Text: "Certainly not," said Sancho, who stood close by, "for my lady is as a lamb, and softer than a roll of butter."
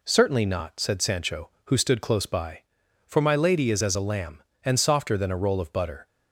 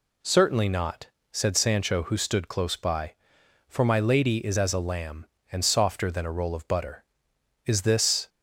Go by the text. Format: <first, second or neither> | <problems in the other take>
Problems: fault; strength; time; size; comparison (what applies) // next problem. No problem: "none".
first | goes on to say "Is this"; noticeable; from 7.6 s on; 0.62 s long